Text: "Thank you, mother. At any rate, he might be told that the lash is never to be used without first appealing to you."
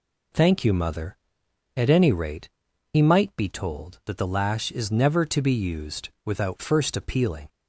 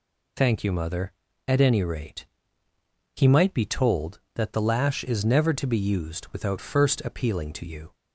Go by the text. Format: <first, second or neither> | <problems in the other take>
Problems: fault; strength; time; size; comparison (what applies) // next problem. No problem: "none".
second | pauses between "used" and "without"; slight; at 6.0 s; 0.16 s long // stops before "to you"; at 7.4 s